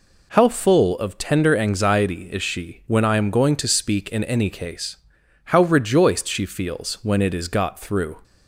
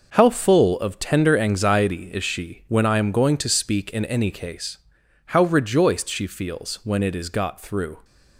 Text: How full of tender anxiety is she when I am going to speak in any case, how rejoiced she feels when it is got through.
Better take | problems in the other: first | gets quieter; strong; throughout; 8.5 dB

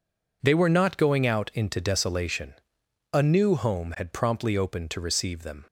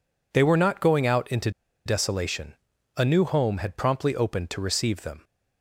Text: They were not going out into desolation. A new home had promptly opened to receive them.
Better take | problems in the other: first | pauses between "into" and "desolation"; slight; at 1.5 s; 0.35 s long

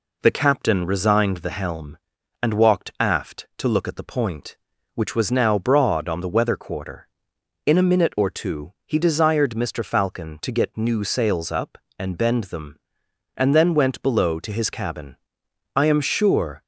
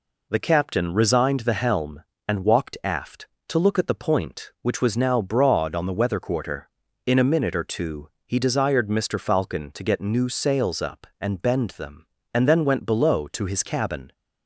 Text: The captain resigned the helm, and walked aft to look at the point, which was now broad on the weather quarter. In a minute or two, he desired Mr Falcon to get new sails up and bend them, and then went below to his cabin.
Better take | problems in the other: second | goes on to say "I am sure"; noticeable; from 15.7 s on; 0.88 s long

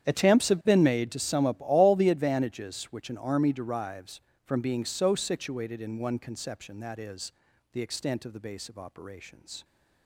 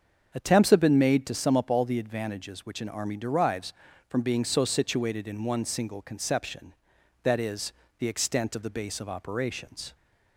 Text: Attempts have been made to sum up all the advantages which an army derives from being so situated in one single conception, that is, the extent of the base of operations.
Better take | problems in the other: second | starts louder than the rest; strong; until 1.1 s; 9.5 dB; also in the second // skips "single"; at 6.1 s

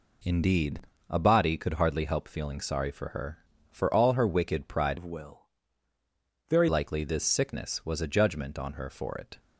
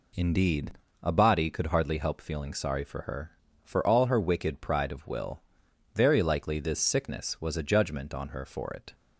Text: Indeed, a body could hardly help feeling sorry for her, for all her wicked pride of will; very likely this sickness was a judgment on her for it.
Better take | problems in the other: second | changes voice from "of" to "very"; from 4.9 to 6.6 s; 1.7 s long

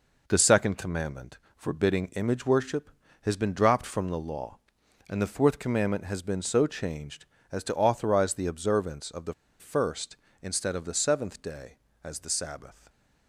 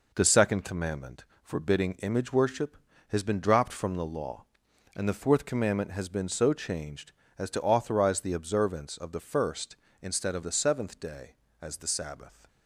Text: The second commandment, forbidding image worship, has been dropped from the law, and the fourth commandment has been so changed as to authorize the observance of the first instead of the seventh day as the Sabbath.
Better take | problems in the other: second | pauses between "the" and "first"; slight; at 9.3 s; 0.25 s long

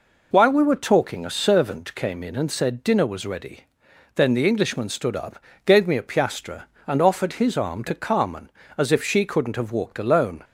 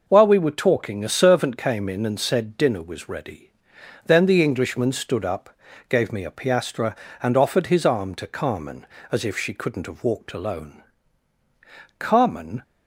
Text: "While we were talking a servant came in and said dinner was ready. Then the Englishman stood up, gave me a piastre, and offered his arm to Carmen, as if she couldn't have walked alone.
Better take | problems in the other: first | goes on to say "Carmen"; noticeable; from 11.9 s on; 0.64 s long

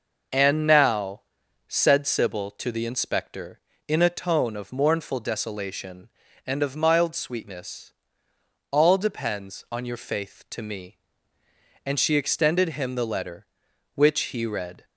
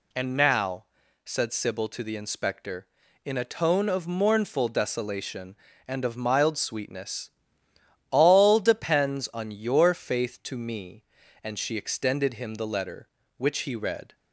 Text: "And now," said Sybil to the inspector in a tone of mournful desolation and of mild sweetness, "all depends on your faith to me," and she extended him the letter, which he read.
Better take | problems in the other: neither | none

